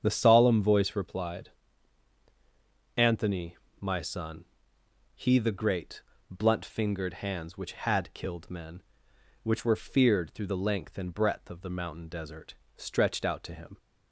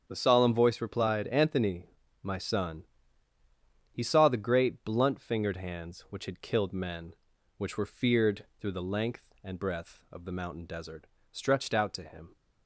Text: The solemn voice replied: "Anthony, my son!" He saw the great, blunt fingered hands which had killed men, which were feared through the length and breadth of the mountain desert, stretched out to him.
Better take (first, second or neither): second